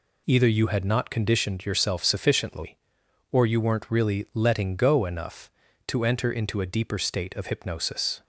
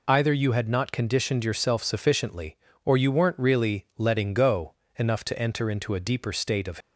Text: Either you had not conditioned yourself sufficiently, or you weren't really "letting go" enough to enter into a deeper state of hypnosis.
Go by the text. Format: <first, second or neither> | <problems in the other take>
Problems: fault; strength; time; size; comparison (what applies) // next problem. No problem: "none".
first | pauses between "go" and "enough"; slight; at 4.7 s; 0.24 s long // stops before "hypnosis"; at 6.8 s